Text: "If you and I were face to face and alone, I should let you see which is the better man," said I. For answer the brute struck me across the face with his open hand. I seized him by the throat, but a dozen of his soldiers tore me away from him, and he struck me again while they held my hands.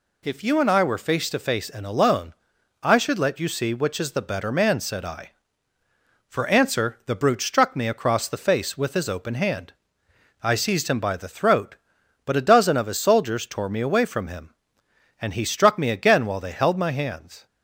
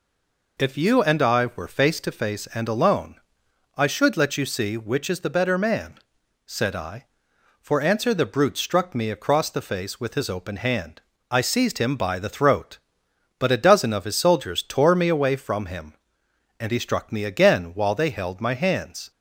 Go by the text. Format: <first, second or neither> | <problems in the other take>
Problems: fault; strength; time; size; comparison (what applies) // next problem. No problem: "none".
first | stays silent before the first word; slight; until 0.5 s; 0.5 s long